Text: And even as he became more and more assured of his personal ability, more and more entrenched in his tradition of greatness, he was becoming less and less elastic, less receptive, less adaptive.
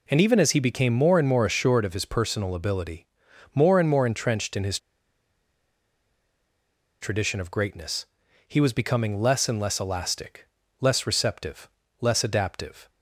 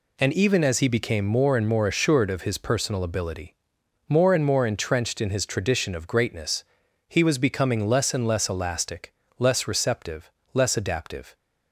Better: second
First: pauses between "his" and "tradition"; strong; at 4.7 s; 2.2 s long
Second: none

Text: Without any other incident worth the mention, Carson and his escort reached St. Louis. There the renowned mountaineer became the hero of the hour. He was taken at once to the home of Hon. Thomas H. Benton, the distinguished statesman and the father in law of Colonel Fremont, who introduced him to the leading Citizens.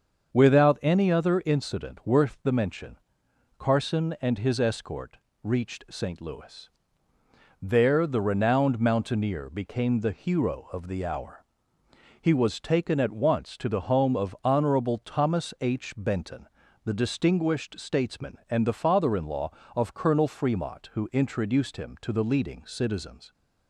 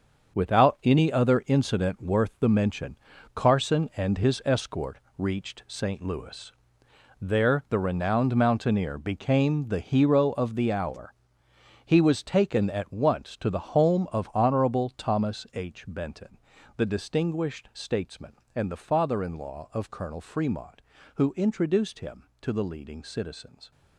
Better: first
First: starts louder than the rest; until 1.3 s; 7 dB // pauses between "escort" and "reached"; slight; at 5.1 s; 0.26 s long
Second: gets quieter; strong; throughout; 10.5 dB // starts louder than the rest; until 1.3 s; 7 dB // pauses between "escort" and "reached"; slight; at 4.9 s; 0.18 s long

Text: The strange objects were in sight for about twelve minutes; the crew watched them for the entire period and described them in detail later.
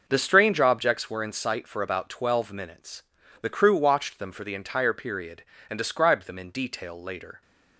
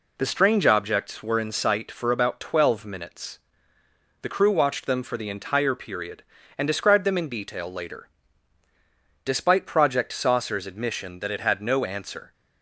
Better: first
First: none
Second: goes on to say "Despite Project Saucer's admission that it had no answer"; strong; from 9.2 s on; 3.0 s long

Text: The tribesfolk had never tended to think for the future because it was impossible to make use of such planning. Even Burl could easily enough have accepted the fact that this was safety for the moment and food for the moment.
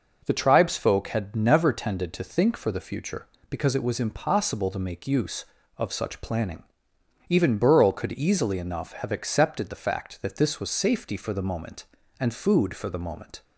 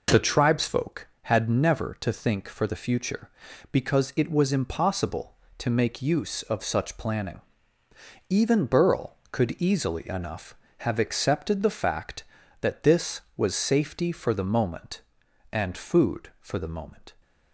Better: first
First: none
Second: skips "tended"; at 1.9 s

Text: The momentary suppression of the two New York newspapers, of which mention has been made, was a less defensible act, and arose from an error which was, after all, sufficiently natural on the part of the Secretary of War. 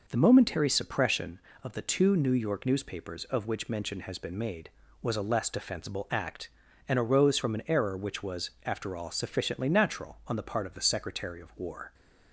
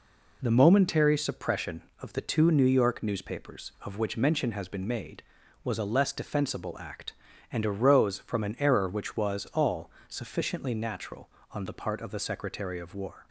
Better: first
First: none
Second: skips "after"; at 9.4 s

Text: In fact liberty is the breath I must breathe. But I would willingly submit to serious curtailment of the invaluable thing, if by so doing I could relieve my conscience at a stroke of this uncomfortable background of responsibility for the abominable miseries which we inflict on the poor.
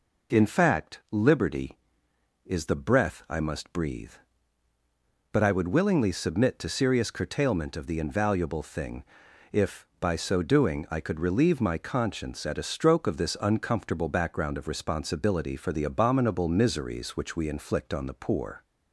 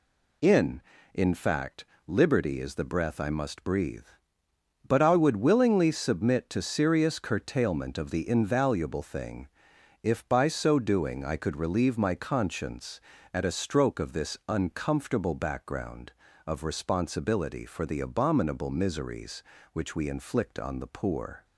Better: first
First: none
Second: says "In" twice; at 1.1 s // pauses between "fact" and "liberty"; slight; at 1.8 s; 0.22 s long

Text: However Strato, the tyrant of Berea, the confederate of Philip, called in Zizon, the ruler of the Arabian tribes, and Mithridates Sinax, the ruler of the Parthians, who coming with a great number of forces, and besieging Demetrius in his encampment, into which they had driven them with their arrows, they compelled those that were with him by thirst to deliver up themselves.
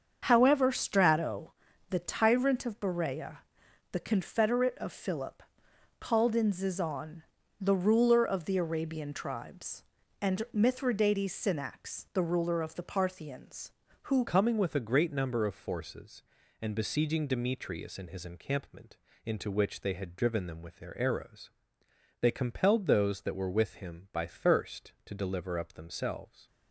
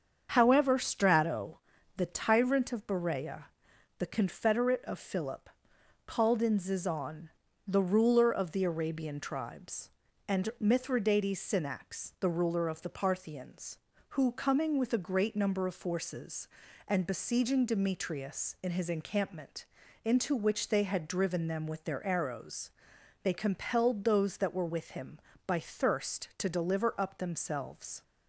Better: second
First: starts louder than the rest; until 1.2 s; 7 dB // changes voice at "coming"; from 14.2 s on; 12.2 s long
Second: starts louder than the rest; until 1.3 s; 7 dB

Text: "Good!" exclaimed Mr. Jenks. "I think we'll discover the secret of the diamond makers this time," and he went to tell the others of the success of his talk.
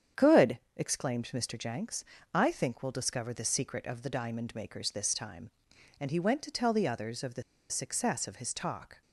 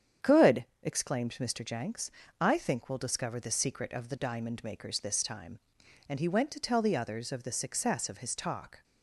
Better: second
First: starts louder than the rest; strong; until 1.3 s; 8.5 dB // pauses between "the" and "success"; slight; at 7.4 s; 0.27 s long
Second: starts louder than the rest; strong; until 1.3 s; 8.5 dB

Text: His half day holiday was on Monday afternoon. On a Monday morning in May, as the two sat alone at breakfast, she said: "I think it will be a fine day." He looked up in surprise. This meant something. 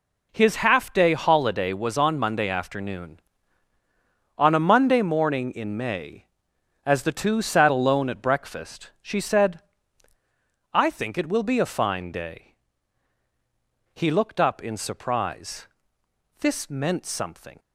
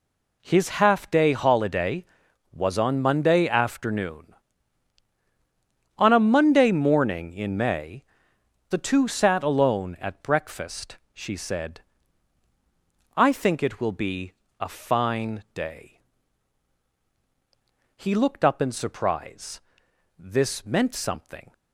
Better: first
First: none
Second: skips "as"; at 8.3 s // pauses between "be" and "a"; slight; at 14.3 s; 0.28 s long

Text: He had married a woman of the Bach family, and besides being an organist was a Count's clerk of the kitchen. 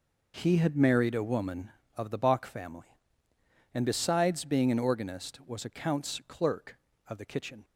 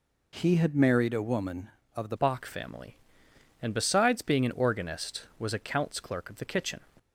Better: first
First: none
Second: changes voice at "Bach"; from 2.1 s on; 4.6 s long

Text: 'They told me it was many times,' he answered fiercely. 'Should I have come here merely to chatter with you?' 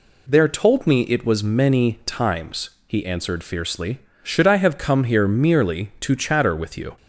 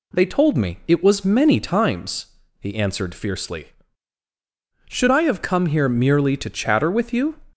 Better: second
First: says "There" for "They"; at 0.2 s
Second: none

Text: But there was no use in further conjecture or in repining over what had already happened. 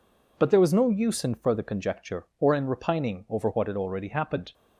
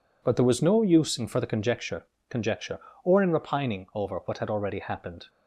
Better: first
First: none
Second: says "conjecture" twice; at 2.2 s

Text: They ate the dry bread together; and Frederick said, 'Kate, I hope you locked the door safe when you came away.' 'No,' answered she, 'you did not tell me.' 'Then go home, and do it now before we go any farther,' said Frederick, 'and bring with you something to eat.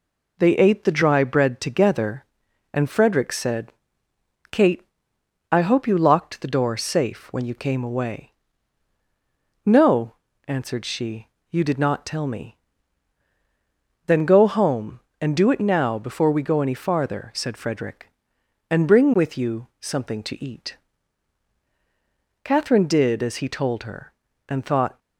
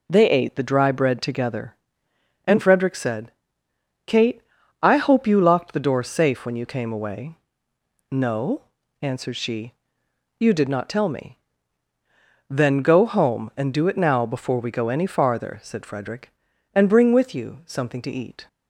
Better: second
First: goes on to say "Catherine did as he told her and thought"; strong; from 22.4 s on; 2.5 s long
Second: none

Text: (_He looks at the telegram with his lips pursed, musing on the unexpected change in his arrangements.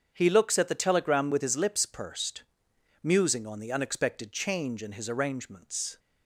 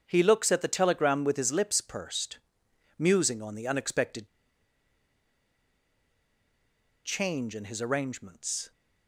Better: first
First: starts louder than the rest; strong; until 1.1 s; 7.5 dB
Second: starts louder than the rest; strong; until 1.0 s; 7.5 dB // pauses between "unexpected" and "change"; strong; at 4.2 s; 2.7 s long

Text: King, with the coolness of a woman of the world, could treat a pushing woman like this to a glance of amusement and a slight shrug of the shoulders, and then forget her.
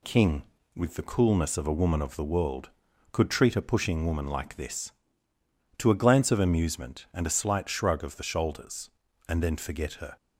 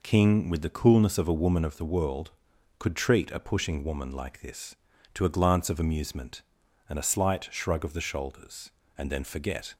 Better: first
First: none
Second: stops before "her"; at 9.7 s

